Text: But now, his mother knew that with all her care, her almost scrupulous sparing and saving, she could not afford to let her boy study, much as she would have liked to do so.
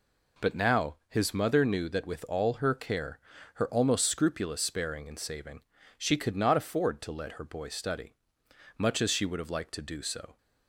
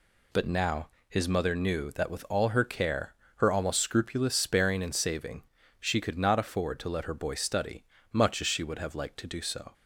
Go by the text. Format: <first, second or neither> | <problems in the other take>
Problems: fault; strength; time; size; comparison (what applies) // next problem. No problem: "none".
neither | none